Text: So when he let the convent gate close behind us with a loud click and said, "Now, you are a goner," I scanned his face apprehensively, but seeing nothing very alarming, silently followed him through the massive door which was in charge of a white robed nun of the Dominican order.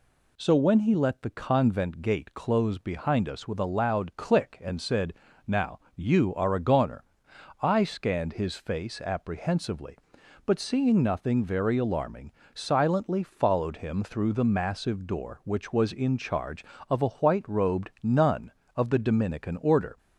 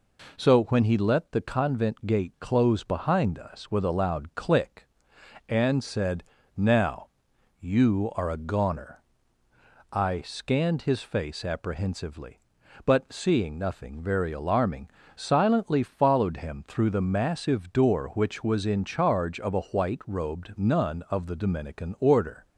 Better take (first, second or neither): neither